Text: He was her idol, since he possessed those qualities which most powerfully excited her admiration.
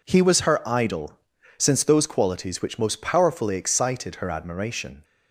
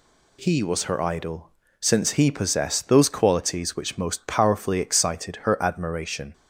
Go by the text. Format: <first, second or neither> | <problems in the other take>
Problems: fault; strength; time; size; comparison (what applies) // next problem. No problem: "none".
second | skips "he possessed"; at 1.8 s